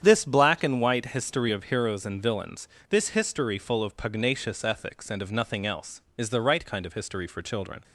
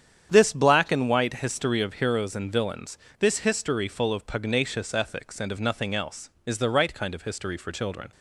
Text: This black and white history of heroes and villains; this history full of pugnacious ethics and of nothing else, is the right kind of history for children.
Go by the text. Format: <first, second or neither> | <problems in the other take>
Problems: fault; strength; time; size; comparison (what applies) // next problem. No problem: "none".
neither | starts louder than the rest; strong; the same in both